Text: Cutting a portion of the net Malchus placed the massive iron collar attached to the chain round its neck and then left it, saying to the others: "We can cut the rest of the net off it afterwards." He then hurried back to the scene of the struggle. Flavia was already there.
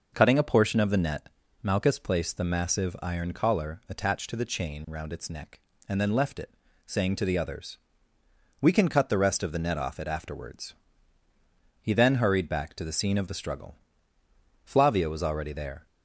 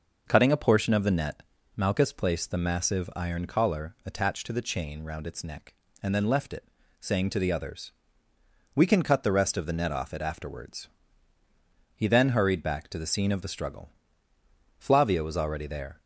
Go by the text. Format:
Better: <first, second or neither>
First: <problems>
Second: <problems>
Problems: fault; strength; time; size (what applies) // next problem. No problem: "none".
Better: neither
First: pauses between "net" and "Malchus"; slight; at 1.2 s; 0.36 s long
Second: pauses between "net" and "Malchus"; slight; at 1.4 s; 0.36 s long